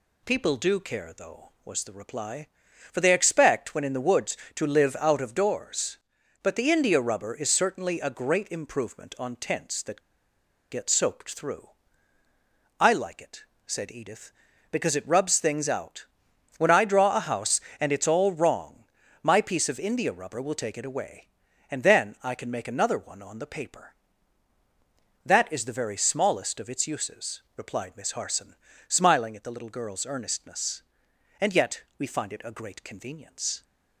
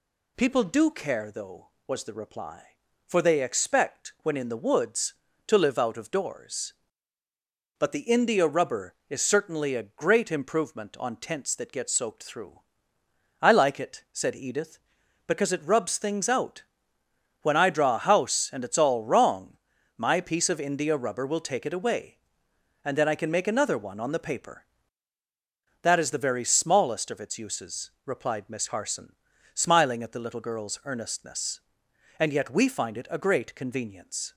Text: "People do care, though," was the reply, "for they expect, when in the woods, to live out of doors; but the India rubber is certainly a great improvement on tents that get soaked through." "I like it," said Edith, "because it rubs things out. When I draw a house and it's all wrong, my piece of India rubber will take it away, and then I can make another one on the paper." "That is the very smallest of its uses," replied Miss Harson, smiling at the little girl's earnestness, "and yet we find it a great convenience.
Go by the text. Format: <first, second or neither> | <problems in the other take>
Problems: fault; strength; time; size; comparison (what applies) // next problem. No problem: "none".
second | pauses between "that" and "get"; noticeable; at 9.9 s; 0.71 s long